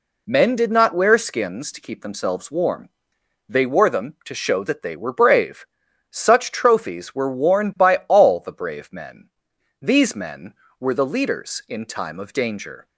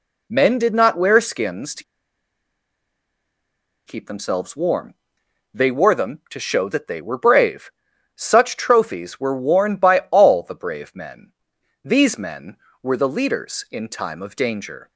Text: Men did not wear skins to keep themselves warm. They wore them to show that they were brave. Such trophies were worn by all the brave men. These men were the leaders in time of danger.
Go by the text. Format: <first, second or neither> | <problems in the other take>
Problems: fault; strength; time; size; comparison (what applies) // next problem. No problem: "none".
first | pauses between "to" and "keep"; strong; at 1.8 s; 2.0 s long